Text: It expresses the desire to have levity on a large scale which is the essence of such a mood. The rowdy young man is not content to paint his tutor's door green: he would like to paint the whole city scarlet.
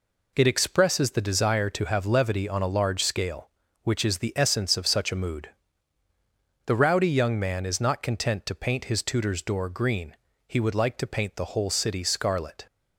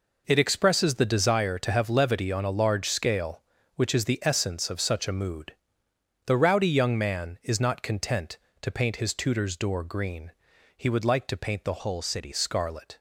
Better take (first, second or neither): first